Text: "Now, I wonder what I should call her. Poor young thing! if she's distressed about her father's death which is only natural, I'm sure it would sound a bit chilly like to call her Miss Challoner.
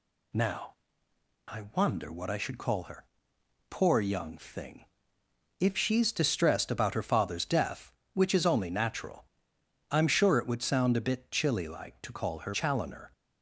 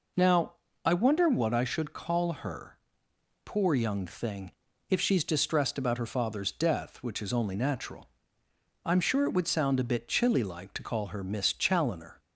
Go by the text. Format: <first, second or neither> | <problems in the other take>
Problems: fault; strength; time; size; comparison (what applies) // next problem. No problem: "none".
second | skips "Miss"; at 12.5 s